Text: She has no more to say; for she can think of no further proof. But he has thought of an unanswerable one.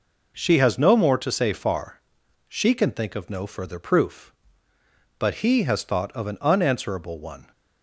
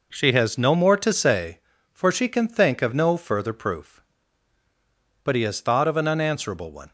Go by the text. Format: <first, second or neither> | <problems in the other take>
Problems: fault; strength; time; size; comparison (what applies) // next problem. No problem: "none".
second | says "far" for "for"; at 1.5 s